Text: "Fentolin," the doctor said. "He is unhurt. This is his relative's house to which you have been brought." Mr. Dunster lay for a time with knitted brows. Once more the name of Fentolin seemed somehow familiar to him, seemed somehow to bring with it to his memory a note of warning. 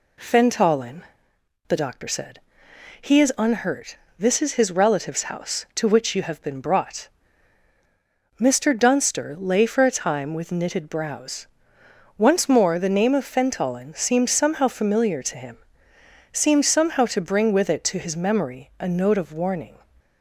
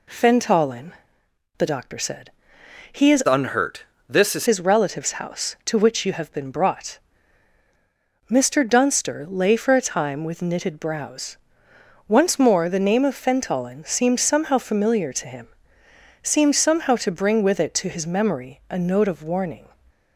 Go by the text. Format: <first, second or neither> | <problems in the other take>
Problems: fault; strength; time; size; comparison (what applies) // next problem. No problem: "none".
first | changes voice from "unhurt" to "is"; from 3.2 to 4.4 s; 1.2 s long